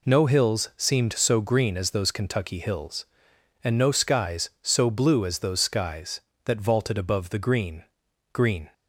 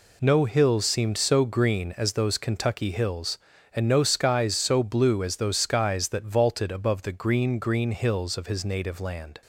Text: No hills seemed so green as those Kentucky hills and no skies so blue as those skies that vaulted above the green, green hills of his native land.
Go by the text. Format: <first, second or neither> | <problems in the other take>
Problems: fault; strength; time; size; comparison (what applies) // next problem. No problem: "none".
second | stops before "hills of his native land"; at 8.7 s